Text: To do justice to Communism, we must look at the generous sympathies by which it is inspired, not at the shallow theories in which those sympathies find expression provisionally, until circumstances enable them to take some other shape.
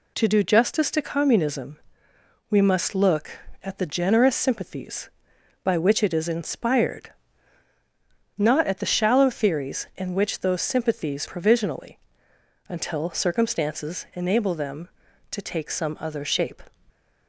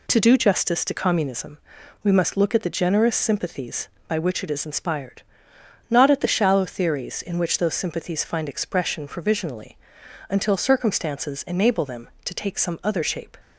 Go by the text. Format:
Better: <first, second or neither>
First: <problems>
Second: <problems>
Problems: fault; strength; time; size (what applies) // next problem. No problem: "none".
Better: second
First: skips "find expression"; at 11.2 s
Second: none